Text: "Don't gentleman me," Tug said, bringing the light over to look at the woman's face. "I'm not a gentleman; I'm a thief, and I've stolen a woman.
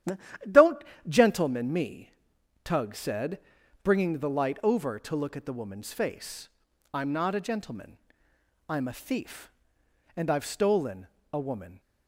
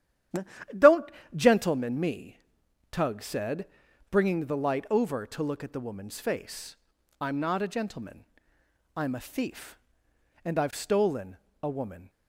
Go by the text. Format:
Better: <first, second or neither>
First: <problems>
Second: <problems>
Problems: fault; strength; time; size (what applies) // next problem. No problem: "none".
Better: neither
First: starts louder than the rest; strong; until 1.7 s; 11.5 dB // pauses between "Don't" and "gentleman"; slight; at 0.8 s; 0.24 s long // pauses between "stolen" and "a"; slight; at 11.0 s; 0.28 s long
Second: starts louder than the rest; strong; until 2.0 s; 11.5 dB // pauses between "Don't" and "gentleman"; slight; at 1.1 s; 0.24 s long // pauses between "stolen" and "a"; slight; at 11.3 s; 0.28 s long